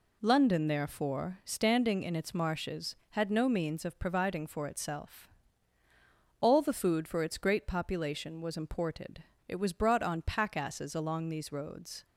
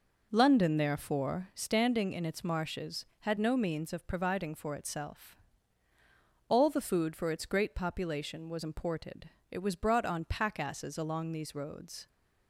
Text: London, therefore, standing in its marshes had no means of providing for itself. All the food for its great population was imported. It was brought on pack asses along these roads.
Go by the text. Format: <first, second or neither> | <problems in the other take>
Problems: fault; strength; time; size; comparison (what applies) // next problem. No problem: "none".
first | starts louder than the rest; noticeable; until 1.6 s; 5.5 dB